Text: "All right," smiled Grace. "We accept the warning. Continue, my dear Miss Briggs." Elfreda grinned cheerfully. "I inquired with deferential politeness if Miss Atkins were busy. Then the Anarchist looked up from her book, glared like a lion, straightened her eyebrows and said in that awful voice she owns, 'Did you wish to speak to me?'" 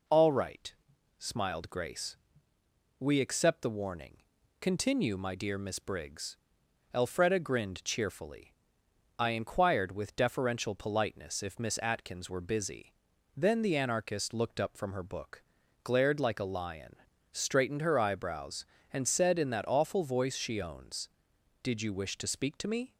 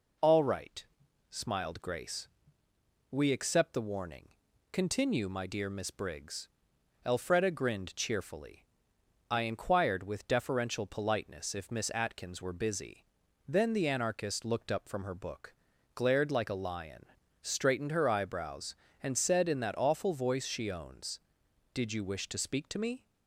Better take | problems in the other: neither | none

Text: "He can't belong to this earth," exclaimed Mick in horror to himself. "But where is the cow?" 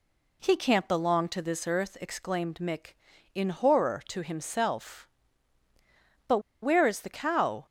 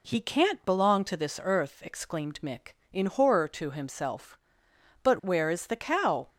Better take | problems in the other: second | pauses between "But" and "where"; slight; at 6.3 s; 0.23 s long

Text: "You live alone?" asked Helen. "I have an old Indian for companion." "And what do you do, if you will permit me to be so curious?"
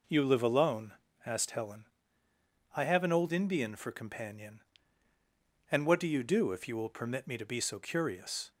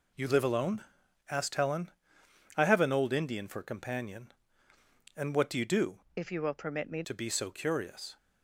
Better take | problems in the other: first | changes voice from "if" to "me"; from 6.1 to 7.0 s; 0.9 s long

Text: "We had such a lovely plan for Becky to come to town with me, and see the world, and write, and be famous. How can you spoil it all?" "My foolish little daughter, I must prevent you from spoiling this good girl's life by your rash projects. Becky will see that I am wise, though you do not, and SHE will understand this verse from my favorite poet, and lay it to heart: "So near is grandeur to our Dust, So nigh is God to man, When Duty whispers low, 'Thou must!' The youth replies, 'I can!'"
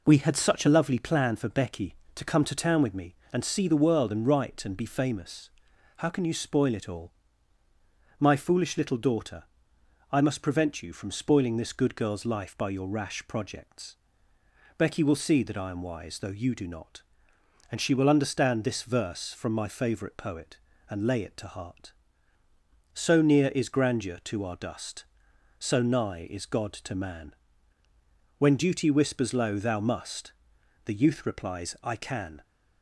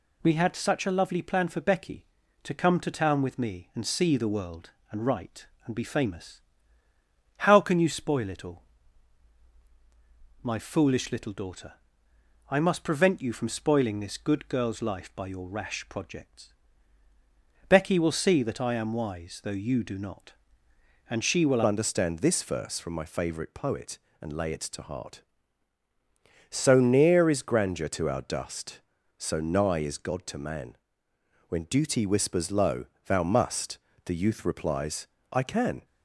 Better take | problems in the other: first | changes voice at "understand"; from 21.6 s on; 14.2 s long

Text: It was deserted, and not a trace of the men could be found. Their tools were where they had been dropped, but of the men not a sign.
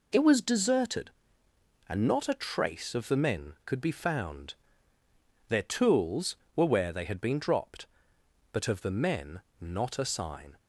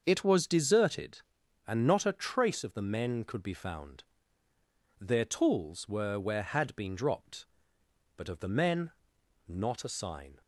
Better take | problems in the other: first | starts louder than the rest; until 1.0 s; 6.5 dB // skips "they"; at 6.4 s // pauses between "men" and "not"; noticeable; at 8.9 s; 0.56 s long; slight in the first

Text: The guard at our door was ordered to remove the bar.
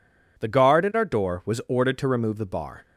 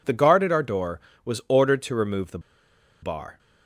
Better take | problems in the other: first | pauses between "the" and "bar"; noticeable; at 2.3 s; 0.62 s long

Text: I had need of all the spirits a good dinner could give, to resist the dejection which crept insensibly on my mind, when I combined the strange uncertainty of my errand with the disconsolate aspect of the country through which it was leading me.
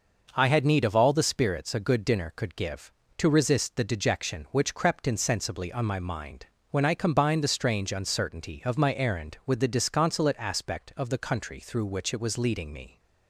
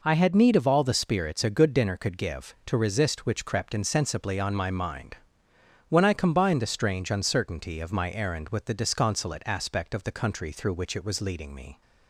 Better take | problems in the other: first | skips "the dejection"; at 3.2 s

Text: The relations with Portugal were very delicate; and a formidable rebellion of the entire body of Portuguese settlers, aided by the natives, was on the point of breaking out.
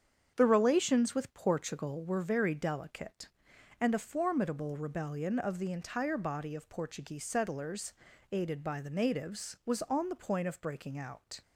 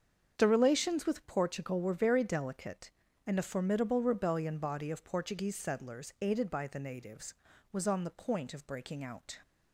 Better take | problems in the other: first | starts louder than the rest; strong; until 1.3 s; 7 dB; strong in the first // skips "of the entire"; at 4.5 s

